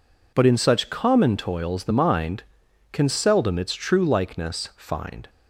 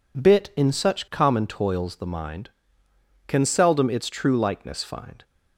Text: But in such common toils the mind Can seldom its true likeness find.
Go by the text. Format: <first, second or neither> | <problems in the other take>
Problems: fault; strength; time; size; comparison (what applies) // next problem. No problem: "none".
first | says "Bit" for "But"; at 0.1 s